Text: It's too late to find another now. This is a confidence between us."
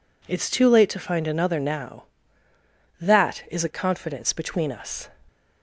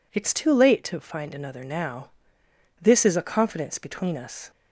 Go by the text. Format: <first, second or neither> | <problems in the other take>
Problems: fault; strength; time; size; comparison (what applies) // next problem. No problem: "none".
second | says "That" for "This"; at 3.0 s